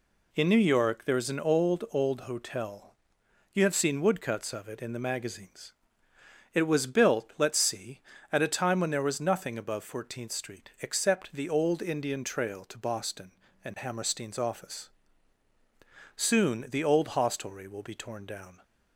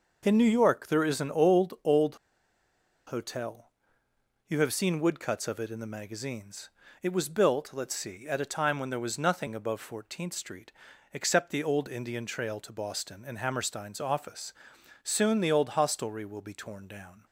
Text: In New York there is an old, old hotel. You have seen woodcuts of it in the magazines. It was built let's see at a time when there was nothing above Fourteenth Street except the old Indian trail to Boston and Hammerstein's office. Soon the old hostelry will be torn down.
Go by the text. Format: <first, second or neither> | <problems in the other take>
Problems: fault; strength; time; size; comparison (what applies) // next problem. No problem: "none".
first | pauses between "old" and "hotel"; noticeable; at 2.1 s; 0.90 s long // pauses between "Street" and "except"; at 10.7 s; 0.42 s long